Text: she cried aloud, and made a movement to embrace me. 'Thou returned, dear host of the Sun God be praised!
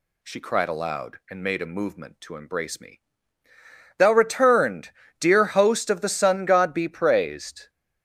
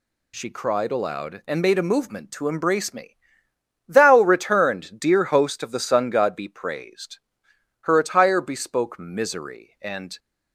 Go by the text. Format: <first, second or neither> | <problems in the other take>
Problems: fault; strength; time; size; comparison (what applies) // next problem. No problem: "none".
first | goes on to say "Her attire bespoke misery and"; strong; from 7.8 s on; 2.3 s long